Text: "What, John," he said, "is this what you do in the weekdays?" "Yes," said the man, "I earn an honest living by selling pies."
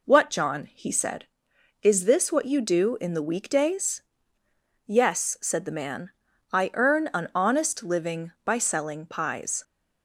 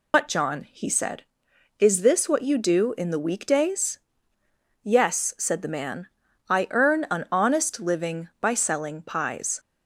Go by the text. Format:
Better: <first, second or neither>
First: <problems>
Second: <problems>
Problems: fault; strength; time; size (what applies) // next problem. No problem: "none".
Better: first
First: none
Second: loses the start of "What"; at 0.1 s; 110 ms